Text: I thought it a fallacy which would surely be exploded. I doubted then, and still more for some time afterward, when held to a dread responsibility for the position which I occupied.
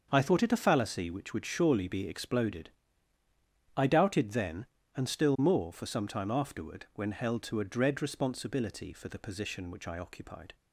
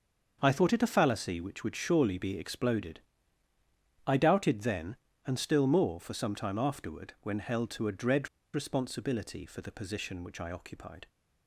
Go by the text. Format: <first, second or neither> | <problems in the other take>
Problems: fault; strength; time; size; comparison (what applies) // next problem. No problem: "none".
first | starts louder than the rest; until 1.4 s; 6.5 dB; also in the first // pauses between "dread" and "responsibility"; slight; at 8.2 s; 0.26 s long